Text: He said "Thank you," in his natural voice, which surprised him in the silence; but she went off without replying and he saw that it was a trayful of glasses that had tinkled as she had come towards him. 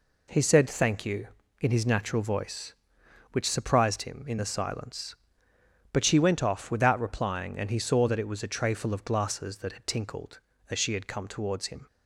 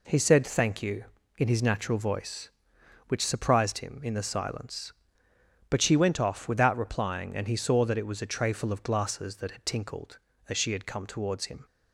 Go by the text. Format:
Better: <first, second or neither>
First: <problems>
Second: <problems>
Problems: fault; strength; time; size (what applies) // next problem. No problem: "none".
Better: neither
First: none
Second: none